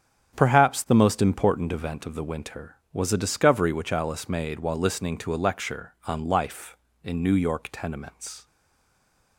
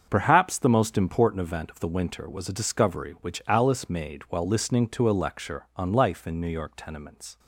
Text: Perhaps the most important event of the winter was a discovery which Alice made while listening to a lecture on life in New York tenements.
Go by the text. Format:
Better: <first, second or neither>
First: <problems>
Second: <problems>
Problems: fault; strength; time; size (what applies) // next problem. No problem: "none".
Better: second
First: starts louder than the rest; strong; until 1.4 s; 8.5 dB // stays silent after the last word; slight; from 8.4 s on; 0.9 s long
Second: starts louder than the rest; until 1.1 s; 7 dB